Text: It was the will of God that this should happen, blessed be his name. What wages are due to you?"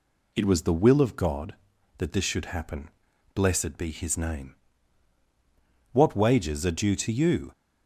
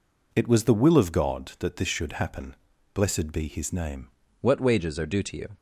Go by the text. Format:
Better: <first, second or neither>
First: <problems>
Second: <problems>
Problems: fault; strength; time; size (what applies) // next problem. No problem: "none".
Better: first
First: none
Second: changes voice at "What"; from 4.4 s on; 1.1 s long